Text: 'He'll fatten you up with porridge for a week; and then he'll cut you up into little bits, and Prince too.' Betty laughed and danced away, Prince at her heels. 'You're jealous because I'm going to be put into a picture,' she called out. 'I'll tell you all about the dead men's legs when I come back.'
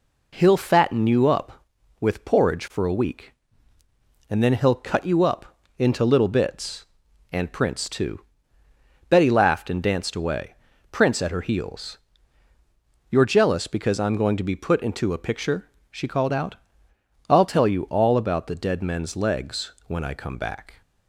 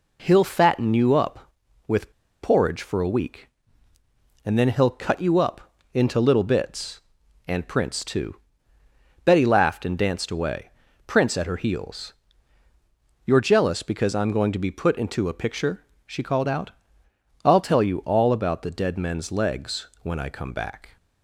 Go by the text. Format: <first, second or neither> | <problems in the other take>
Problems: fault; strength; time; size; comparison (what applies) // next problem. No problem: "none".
first | pauses between "with" and "porridge"; slight; at 2.1 s; 0.31 s long // pauses between "up" and "into"; slight; at 5.6 s; 0.34 s long; slight in the first // pauses between "legs" and "when"; slight; at 19.8 s; 0.16 s long; slight in the first